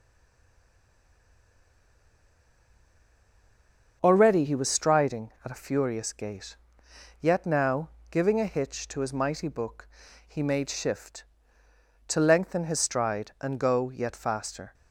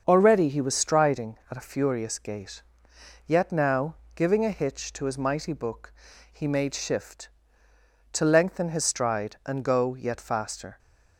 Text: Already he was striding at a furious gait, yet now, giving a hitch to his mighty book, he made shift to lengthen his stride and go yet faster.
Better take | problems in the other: second | stays silent before the first word; strong; until 4.0 s; 4.0 s long // starts louder than the rest; until 5.0 s; 7 dB; also in the second

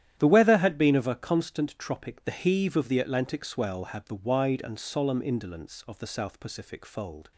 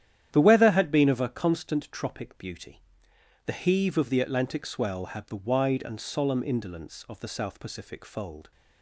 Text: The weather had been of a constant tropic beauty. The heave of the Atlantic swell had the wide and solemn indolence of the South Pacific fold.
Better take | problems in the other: second | starts louder than the rest; strong; until 1.2 s; 11.5 dB; strong in the second // skips "beauty"; at 2.2 s

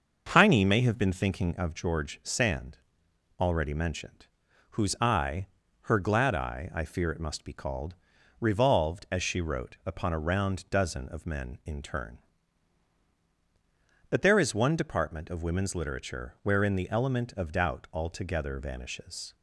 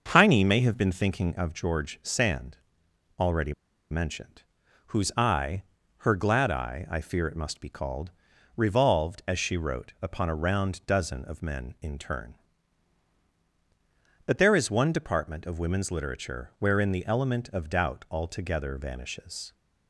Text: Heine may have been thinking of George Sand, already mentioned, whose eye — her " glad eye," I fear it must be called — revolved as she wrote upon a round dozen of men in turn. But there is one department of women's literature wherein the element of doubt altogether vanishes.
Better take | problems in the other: first | starts louder than the rest; until 1.1 s; 6.5 dB; also in the first // pauses between "already" and "mentioned"; at 3.5 s; 0.38 s long

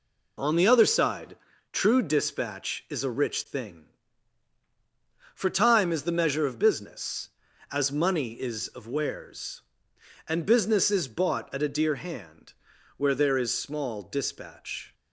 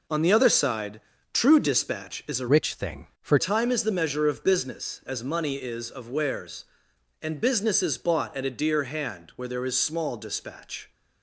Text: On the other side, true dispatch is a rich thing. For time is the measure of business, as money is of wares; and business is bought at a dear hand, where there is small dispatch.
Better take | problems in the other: first | changes voice from "rich" to "For"; from 2.4 to 3.3 s; 0.9 s long

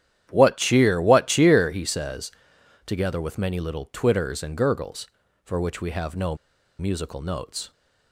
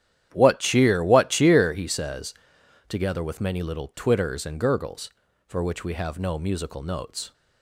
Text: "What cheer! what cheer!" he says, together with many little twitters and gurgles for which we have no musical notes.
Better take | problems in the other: second | starts louder than the rest; strong; until 1.3 s; 10.5 dB; strong in the second // pauses between "no" and "musical"; at 6.3 s; 0.43 s long

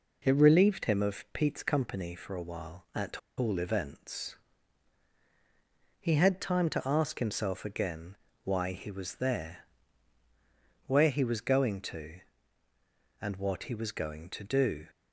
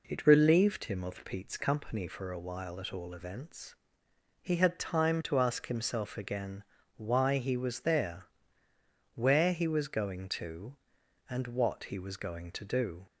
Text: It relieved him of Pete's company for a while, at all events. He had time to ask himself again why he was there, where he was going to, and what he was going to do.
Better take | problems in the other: second | pauses between "at" and "all"; slight; at 3.1 s; 0.18 s long // pauses between "again" and "why"; slight; at 8.1 s; 0.28 s long; slight in the second

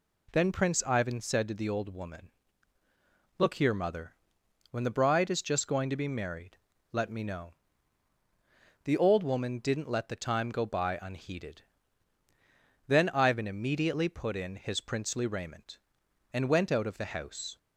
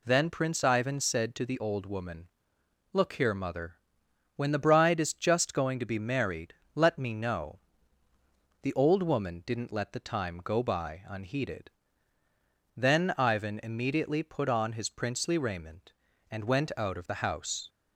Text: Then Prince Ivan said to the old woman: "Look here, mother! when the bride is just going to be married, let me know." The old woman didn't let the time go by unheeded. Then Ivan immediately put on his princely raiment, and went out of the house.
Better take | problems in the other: second | says "in" for "on"; at 14.3 s

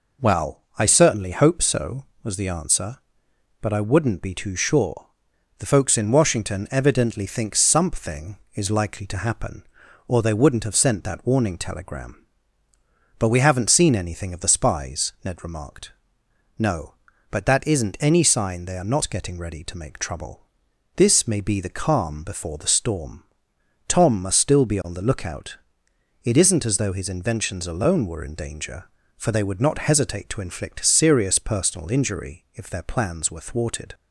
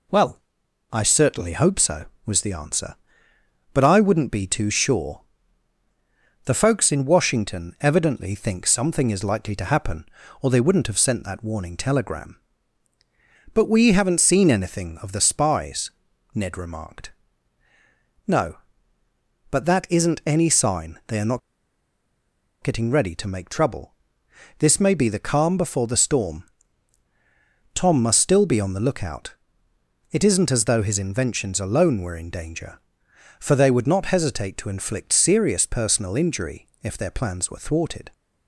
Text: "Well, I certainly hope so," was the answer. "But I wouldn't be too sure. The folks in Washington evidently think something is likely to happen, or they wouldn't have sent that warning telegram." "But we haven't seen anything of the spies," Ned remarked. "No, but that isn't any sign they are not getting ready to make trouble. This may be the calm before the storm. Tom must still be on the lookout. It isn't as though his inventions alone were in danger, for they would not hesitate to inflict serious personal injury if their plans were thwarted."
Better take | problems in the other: first | pauses between "not" and "getting"; at 21.3 s; 1.2 s long // pauses between "injury" and "if"; slight; at 36.6 s; 0.18 s long

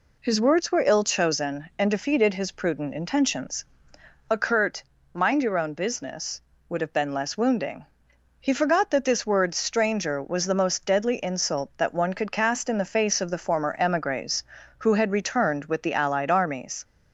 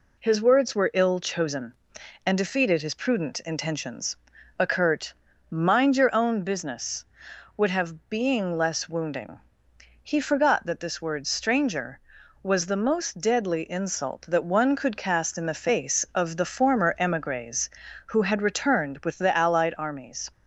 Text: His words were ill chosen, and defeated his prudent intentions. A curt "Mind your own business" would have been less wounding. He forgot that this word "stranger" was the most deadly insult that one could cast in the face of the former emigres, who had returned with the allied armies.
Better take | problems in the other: first | pauses between "curt" and "Mind"; at 5.1 s; 0.38 s long; slight in the first // says "being" for "been"; at 8.0 s

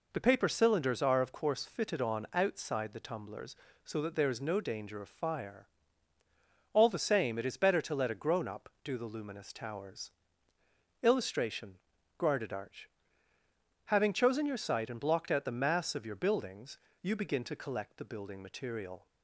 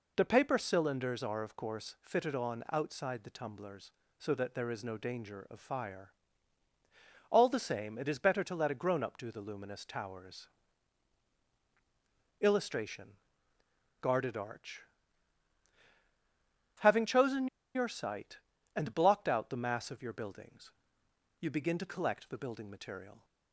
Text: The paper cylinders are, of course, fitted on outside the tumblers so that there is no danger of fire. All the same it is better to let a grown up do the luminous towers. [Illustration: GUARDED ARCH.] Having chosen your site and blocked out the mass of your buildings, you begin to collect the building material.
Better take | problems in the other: first | pauses between "chosen" and "your"; slight; at 17.4 s; 0.26 s long

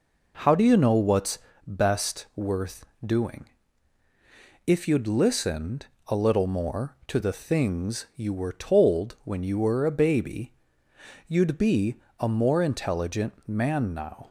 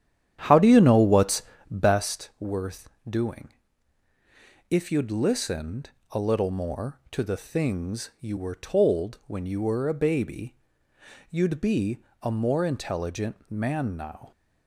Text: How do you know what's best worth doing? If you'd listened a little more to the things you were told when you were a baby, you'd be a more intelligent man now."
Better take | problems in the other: first | starts louder than the rest; strong; until 2.1 s; 10 dB // pauses between "what's" and "best"; slight; at 1.4 s; 0.26 s long; slight in the first // pauses between "worth" and "doing"; slight; at 2.8 s; 0.18 s long; slight in the first // pauses between "listened" and "a"; slight; at 5.8 s; 0.22 s long; slight in the first // pauses between "be" and "a"; slight; at 11.9 s; 0.24 s long; slight in the first

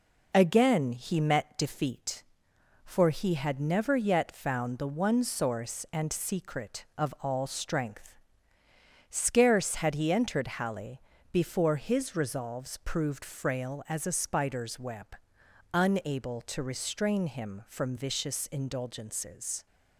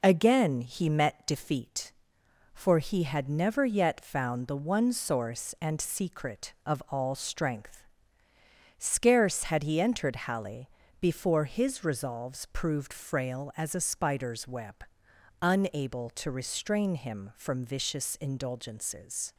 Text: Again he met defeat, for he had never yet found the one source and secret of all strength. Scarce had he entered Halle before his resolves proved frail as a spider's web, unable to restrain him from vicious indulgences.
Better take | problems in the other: neither | pauses between "Halle" and "before"; slight; the same in both

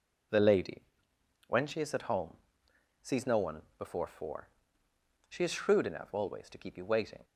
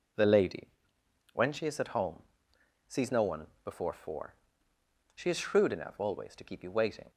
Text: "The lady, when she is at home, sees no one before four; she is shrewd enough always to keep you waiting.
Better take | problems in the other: neither | pauses between "one" and "before"; slight; the same in both

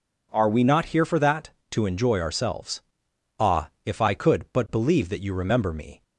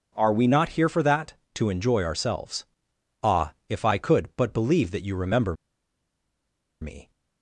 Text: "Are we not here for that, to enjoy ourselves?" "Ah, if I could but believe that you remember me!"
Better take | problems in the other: first | pauses between "remember" and "me"; strong; at 5.5 s; 1.2 s long

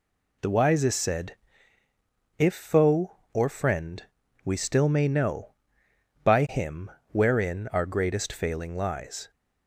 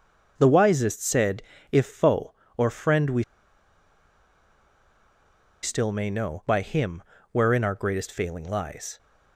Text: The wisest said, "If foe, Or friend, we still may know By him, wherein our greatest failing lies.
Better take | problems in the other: first | pauses between "we" and "still"; strong; at 3.2 s; 2.3 s long

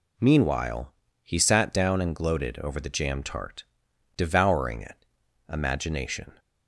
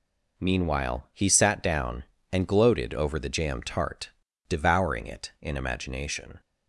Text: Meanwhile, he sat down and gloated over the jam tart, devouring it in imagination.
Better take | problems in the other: second | skips "in"; at 5.2 s

